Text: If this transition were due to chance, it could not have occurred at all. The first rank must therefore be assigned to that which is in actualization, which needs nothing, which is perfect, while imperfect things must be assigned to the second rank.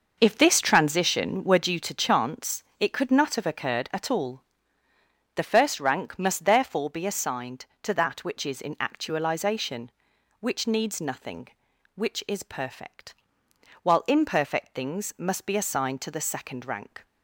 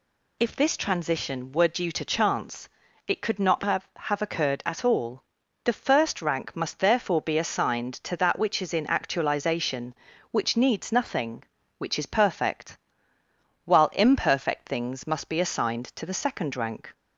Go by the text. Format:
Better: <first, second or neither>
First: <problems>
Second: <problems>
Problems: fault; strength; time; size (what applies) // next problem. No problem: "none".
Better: first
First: none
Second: says "have" twice; at 3.9 s